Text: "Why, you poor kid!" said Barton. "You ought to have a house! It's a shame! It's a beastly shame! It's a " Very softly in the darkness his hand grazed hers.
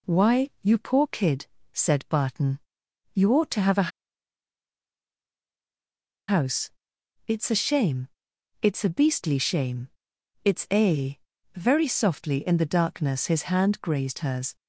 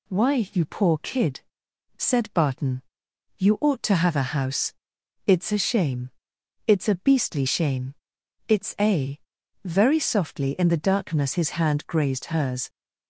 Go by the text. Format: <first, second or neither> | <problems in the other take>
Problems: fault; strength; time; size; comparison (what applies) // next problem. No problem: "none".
second | pauses between "a" and "house"; strong; at 3.9 s; 2.4 s long